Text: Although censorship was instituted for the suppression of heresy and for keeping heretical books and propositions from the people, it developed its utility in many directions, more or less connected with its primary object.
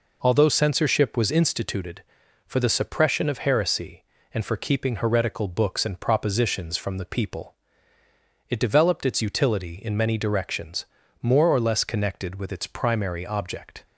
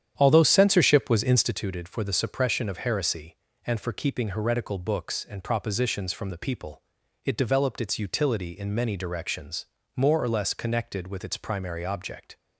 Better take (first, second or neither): first